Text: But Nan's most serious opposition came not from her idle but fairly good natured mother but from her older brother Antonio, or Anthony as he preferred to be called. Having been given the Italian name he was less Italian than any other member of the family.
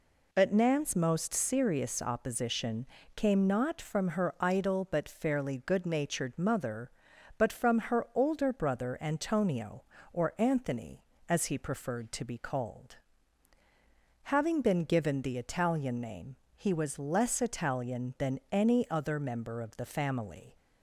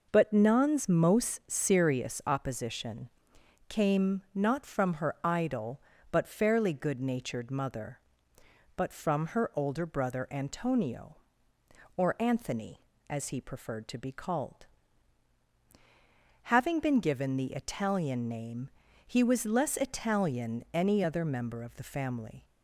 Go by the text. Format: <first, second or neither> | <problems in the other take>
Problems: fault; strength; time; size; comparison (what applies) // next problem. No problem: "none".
first | pauses between "opposition" and "came"; noticeable; at 3.0 s; 0.60 s long; slight in the first // pauses between "name" and "he"; slight; at 18.7 s; 0.36 s long; slight in the first // skips "than"; at 20.6 s